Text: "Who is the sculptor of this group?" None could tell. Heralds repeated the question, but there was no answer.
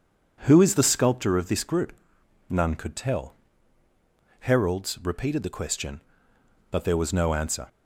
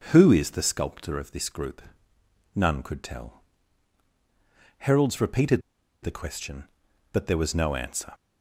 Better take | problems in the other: first | starts louder than the rest; until 1.1 s; 6 dB // pauses between "repeated" and "the"; at 5.6 s; 0.42 s long

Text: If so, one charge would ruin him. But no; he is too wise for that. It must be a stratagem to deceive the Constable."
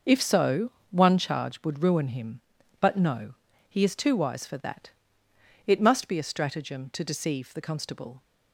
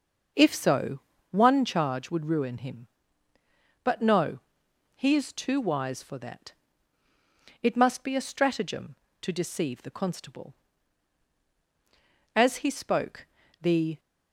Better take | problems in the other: first | starts louder than the rest; until 1.6 s; 6.5 dB // goes on to say "As he spoke the"; from 12.3 s on; 1.6 s long

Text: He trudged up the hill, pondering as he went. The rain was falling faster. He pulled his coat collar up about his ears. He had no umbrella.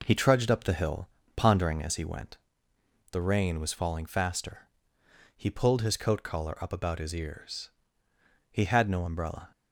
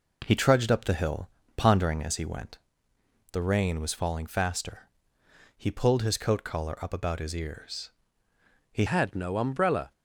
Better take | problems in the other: first | changes voice at "had"; from 8.8 s on; 1.1 s long

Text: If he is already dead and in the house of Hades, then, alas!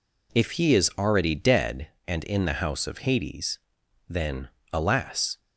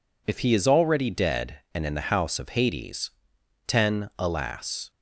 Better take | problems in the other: first | says "ten" for "then"; at 3.6 s

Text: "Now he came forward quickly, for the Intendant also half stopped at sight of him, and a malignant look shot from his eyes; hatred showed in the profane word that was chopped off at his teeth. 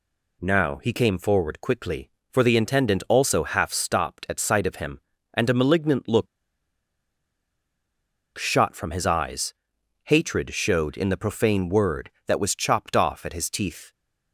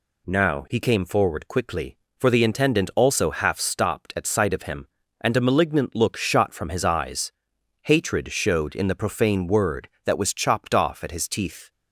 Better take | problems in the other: second | pauses between "look" and "shot"; strong; at 6.2 s; 2.1 s long

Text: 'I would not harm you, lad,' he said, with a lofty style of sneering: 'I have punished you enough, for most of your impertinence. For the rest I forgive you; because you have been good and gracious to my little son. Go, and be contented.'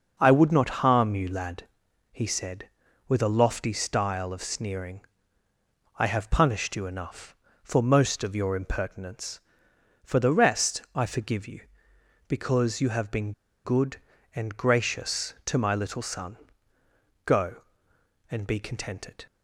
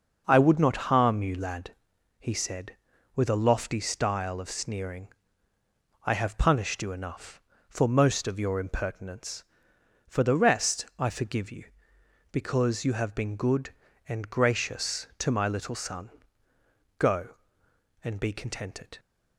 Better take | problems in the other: second | pauses between "been" and "good"; slight; at 13.3 s; 0.33 s long

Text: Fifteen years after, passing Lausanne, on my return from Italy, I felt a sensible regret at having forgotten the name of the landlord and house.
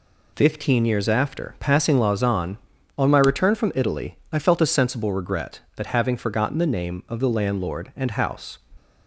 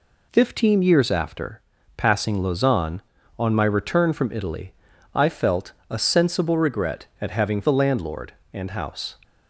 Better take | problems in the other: first | pauses between "felt" and "a"; slight; at 5.7 s; 0.16 s long // skips "forgotten the name of"; at 7.6 s

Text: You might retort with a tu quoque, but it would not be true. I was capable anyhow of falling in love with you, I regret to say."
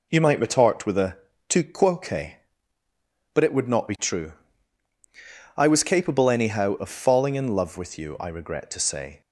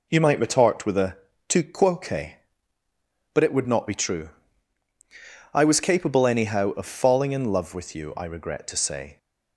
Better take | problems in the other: neither | pauses between "a" and "tu"; slight; the same in both

